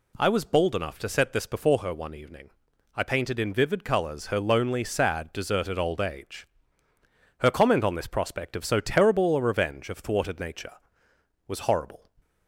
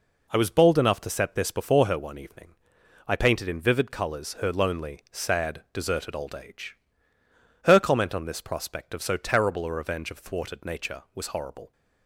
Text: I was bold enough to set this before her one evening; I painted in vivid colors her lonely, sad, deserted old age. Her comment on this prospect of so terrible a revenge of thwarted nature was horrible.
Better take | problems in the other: neither | none

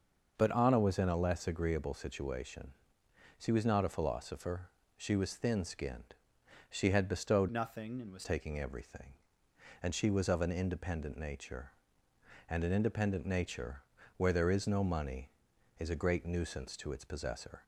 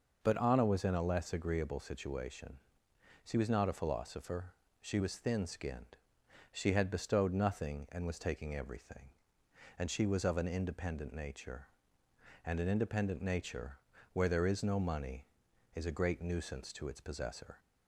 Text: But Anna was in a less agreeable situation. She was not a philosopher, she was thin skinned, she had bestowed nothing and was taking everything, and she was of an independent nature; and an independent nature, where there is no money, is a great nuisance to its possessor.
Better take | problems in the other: second | starts louder than the rest; noticeable; until 1.3 s; 6 dB // changes voice from "nothing" to "was"; from 7.4 to 8.2 s; 0.8 s long

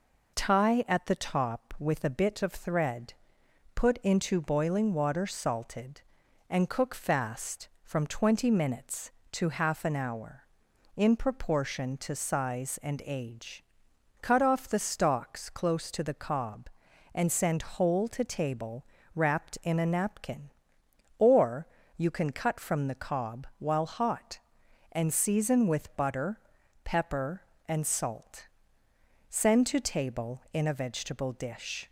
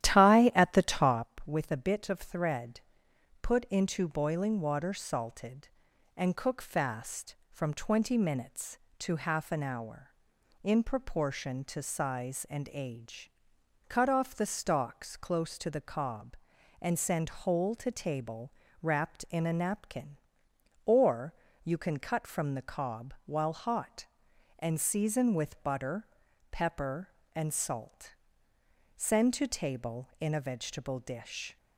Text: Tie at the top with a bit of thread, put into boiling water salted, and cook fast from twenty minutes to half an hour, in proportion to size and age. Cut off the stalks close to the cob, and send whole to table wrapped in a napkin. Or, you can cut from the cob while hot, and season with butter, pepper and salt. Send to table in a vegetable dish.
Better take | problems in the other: first | starts louder than the rest; strong; until 1.3 s; 12 dB // pauses between "table" and "wrapped"; slight; at 18.5 s; 0.28 s long; slight in the first

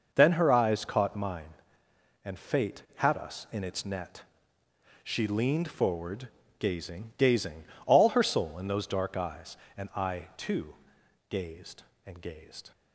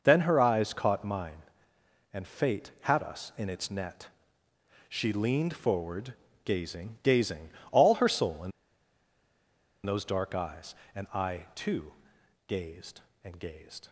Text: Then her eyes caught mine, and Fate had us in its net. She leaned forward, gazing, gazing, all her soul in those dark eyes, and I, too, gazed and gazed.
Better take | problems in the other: first | pauses between "in" and "those"; strong; at 8.5 s; 1.3 s long

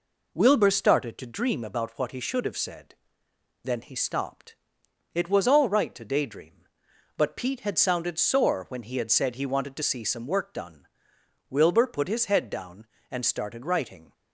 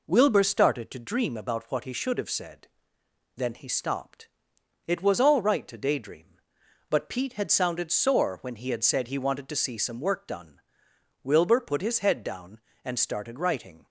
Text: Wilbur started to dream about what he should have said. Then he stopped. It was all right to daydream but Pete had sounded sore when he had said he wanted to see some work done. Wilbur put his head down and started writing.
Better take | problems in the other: neither | none

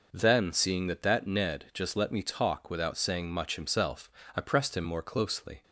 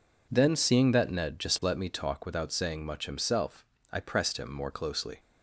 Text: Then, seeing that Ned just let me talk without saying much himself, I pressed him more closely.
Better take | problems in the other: second | says "that" twice; at 1.0 s

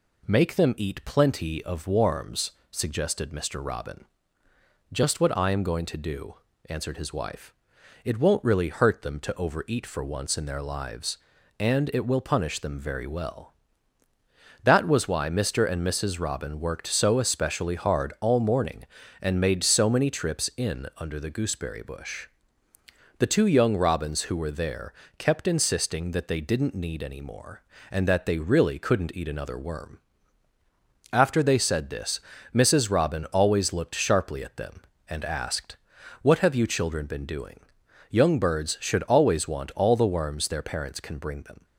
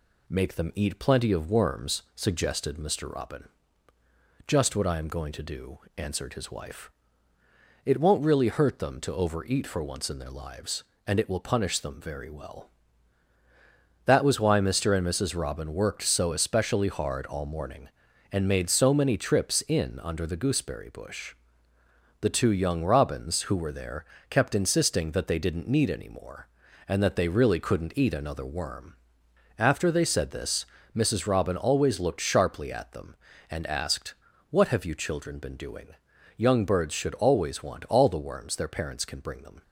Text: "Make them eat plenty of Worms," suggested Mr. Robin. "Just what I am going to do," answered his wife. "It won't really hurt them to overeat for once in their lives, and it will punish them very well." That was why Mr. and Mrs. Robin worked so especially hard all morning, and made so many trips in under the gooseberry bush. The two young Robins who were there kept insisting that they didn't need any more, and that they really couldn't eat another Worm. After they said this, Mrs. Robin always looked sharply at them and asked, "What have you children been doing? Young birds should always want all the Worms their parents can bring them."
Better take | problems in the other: neither | pauses between "there" and "kept"; slight; the same in both

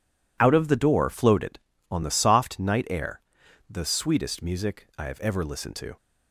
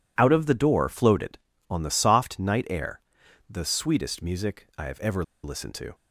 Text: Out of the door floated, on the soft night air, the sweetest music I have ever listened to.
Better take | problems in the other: first | pauses between "ever" and "listened"; slight; at 5.2 s; 0.21 s long

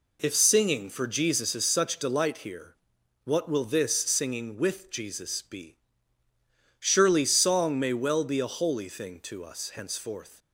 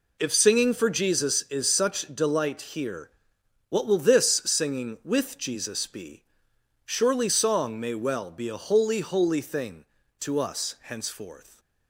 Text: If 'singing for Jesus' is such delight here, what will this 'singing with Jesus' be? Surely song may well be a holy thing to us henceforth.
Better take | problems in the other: first | says "holy" twice; at 8.9 s

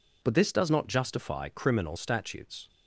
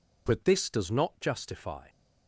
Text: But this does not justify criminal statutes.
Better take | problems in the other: first | stops before "criminal statutes"; at 1.8 s

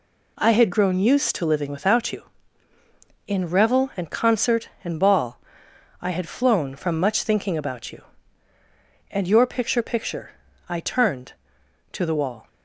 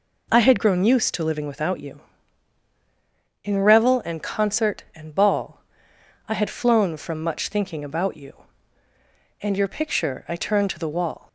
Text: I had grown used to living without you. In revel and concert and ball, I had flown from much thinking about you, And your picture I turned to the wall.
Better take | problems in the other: second | says "picture" twice; at 9.8 s

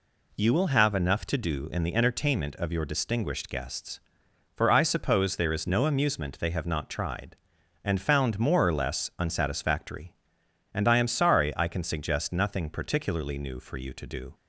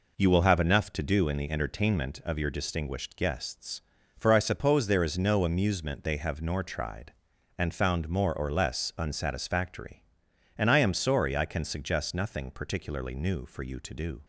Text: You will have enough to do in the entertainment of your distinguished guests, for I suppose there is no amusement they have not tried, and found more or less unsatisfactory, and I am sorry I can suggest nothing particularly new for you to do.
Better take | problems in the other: first | says "nor" for "not"; at 6.4 s

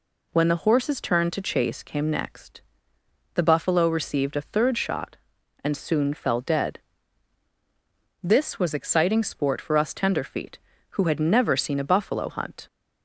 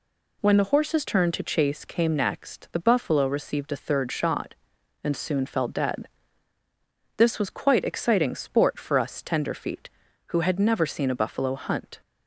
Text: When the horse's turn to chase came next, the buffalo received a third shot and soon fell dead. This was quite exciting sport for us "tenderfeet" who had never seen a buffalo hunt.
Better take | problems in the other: second | skips "quite"; at 8.7 s

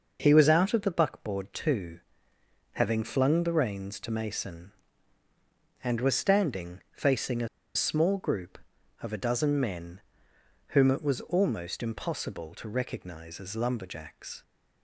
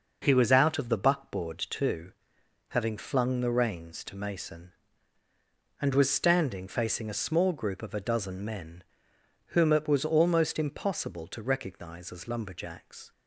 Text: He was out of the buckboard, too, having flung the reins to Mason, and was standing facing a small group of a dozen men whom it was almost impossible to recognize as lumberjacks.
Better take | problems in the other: second | pauses between "a" and "small"; slight; at 7.4 s; 0.27 s long // pauses between "men" and "whom"; noticeable; at 9.9 s; 0.68 s long; noticeable in the second

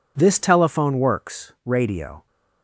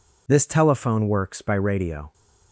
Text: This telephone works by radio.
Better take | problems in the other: second | skips "by"; at 1.5 s

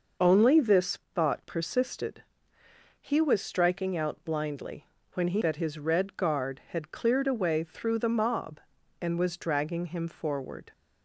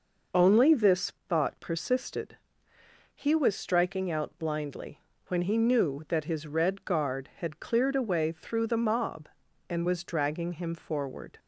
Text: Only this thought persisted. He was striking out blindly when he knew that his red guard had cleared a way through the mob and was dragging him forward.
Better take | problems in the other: second | pauses between "this" and "thought"; slight; at 0.9 s; 0.16 s long; slight in the second // pauses between "blindly" and "when"; slight; at 4.8 s; 0.26 s long; slight in the second // skips "knew"; at 5.4 s

